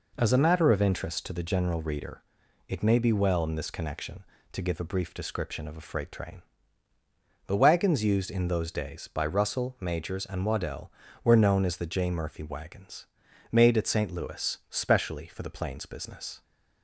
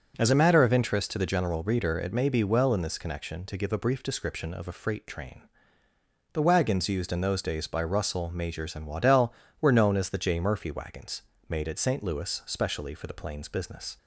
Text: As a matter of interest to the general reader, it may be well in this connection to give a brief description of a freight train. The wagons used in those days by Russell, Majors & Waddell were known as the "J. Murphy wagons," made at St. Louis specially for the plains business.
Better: neither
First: none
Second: none

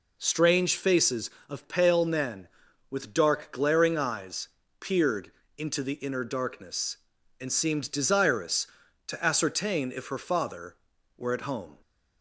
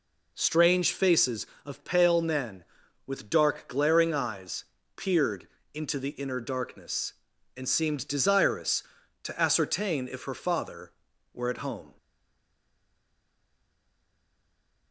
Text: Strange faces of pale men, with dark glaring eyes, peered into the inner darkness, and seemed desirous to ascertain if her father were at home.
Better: first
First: pauses between "peered" and "into"; slight; at 5.2 s; 0.28 s long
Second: pauses between "peered" and "into"; slight; at 5.4 s; 0.28 s long // stays silent after the last word; strong; from 11.9 s on; 3.0 s long

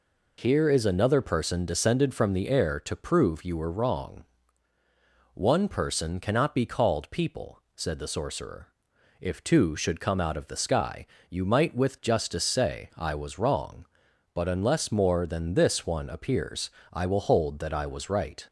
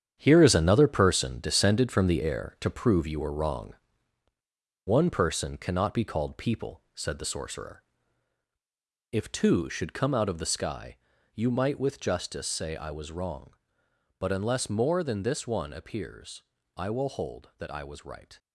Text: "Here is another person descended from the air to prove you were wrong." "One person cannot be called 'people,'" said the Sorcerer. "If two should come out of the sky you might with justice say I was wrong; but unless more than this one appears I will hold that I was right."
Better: first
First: pauses between "sky" and "you"; slight; at 11.0 s; 0.22 s long // pauses between "appears" and "I"; slight; at 16.7 s; 0.22 s long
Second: gets quieter; strong; throughout; 9.5 dB // pauses between "sky" and "you"; at 10.9 s; 0.38 s long // pauses between "appears" and "I"; slight; at 16.4 s; 0.34 s long

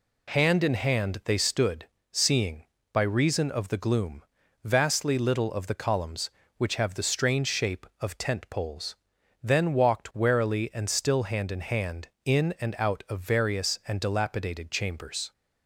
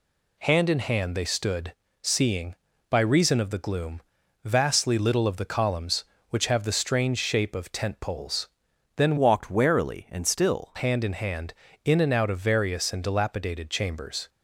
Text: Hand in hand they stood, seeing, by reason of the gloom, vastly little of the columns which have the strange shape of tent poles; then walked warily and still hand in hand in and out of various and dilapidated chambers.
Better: first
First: none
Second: changes voice from "walked" to "still"; from 9.1 to 10.7 s; 1.6 s long

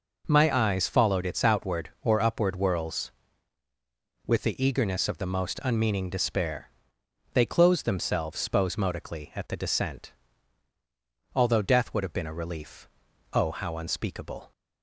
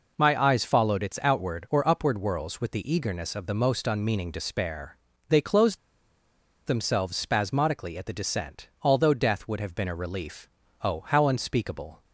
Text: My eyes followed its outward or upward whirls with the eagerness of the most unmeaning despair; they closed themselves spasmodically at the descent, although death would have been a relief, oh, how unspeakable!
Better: first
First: none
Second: pauses between "closed" and "themselves"; noticeable; at 5.7 s; 0.89 s long

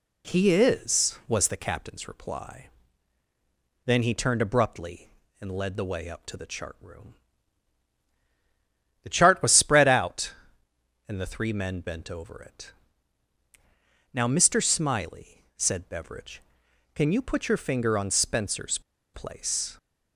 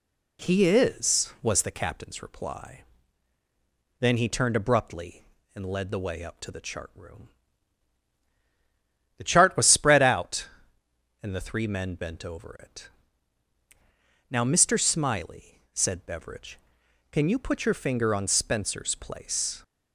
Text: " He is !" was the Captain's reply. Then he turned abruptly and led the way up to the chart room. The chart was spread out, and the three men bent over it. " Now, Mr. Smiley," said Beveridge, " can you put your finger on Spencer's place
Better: second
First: pauses between "Spencer's" and "place"; slight; at 18.7 s; 0.34 s long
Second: none

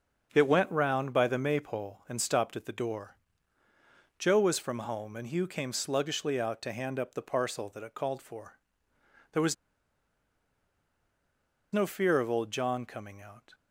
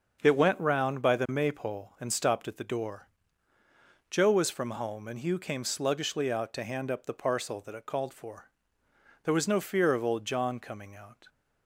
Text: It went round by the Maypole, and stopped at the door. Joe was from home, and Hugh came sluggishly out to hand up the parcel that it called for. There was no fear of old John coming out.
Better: second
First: starts louder than the rest; until 1.3 s; 6.5 dB // pauses between "was" and "no"; strong; at 9.5 s; 2.1 s long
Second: starts louder than the rest; until 1.2 s; 6.5 dB

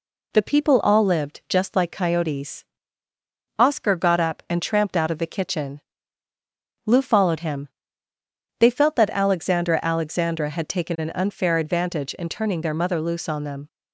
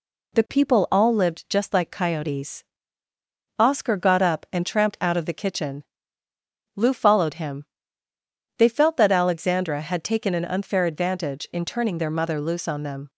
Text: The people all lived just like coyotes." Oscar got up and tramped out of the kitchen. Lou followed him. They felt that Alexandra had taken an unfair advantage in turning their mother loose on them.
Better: second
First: says "Alexandra" twice; at 9.8 s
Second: none

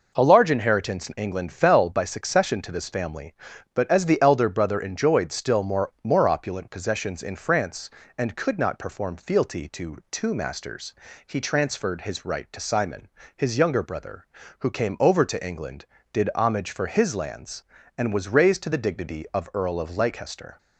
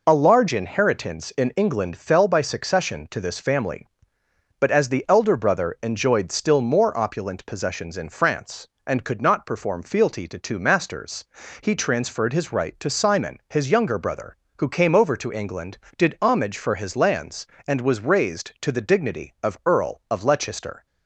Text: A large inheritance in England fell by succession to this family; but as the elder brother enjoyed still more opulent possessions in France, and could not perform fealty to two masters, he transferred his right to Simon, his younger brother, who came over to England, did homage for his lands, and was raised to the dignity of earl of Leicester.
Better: second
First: says "more" twice; at 6.0 s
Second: none

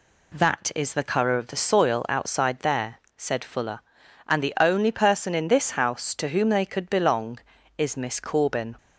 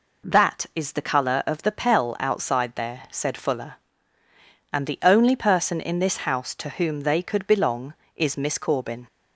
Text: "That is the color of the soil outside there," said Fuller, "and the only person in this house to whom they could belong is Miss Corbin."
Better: first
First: none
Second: says "pell" for "soil"; at 1.7 s

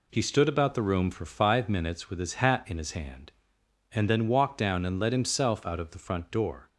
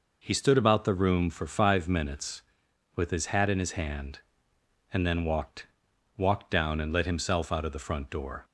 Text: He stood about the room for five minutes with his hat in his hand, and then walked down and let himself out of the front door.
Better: first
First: none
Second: says "walked" twice; at 6.1 s

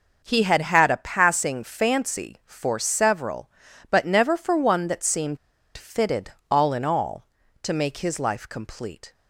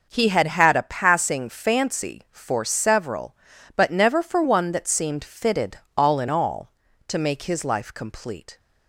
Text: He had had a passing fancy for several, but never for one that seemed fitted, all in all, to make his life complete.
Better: second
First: pauses between "seemed" and "fitted"; at 5.3 s; 0.39 s long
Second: none

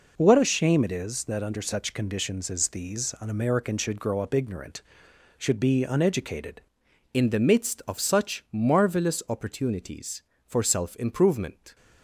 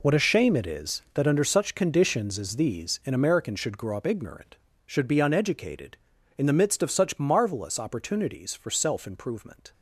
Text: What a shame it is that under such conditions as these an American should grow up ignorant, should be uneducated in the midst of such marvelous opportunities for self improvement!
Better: second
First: changes voice at "in"; from 7.1 s on; 4.6 s long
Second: none

